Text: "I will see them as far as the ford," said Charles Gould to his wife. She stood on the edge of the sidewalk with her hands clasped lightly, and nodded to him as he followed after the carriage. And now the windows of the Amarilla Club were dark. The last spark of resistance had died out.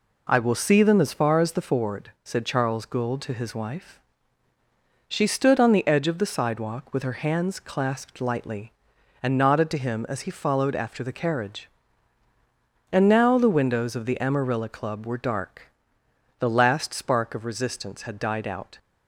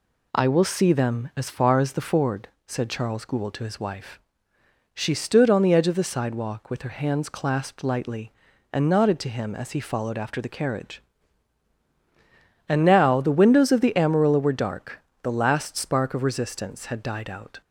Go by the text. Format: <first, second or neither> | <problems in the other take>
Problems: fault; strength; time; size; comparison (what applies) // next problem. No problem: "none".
first | skips "Club"; at 14.3 s